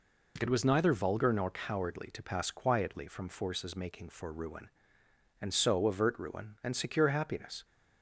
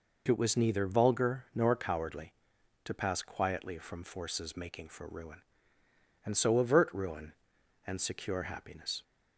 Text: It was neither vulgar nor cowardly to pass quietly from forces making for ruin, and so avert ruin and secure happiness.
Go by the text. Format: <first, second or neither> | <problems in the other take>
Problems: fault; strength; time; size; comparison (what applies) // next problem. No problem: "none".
neither | none